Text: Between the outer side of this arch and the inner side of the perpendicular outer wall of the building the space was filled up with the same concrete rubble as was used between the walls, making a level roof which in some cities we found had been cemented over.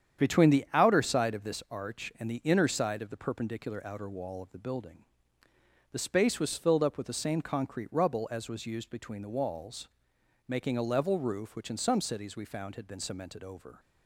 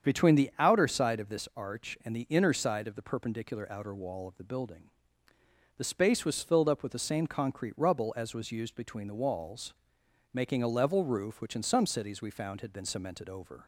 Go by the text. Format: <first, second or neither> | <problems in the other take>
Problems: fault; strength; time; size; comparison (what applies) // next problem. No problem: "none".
second | gets quieter; throughout; 7 dB // starts louder than the rest; strong; until 1.2 s; 8.5 dB; strong in the second // pauses between "building" and "the"; noticeable; at 5.0 s; 0.86 s long; noticeable in the second